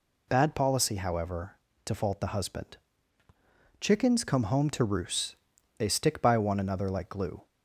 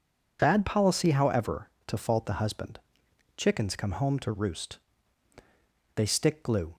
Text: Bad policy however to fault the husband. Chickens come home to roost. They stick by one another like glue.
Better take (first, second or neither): first